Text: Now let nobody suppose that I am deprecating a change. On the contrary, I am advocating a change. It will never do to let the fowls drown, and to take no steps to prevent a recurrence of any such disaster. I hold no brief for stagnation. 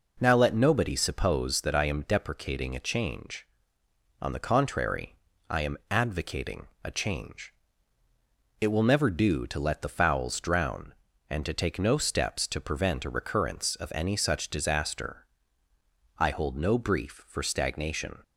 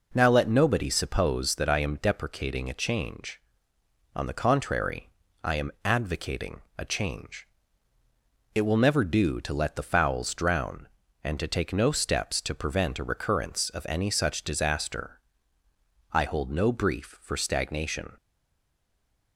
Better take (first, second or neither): first